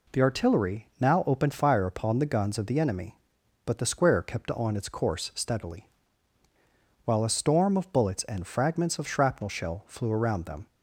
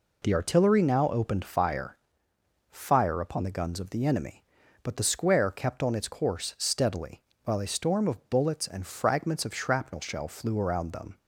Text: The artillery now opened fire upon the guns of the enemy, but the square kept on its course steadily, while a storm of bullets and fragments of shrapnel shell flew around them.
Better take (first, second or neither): first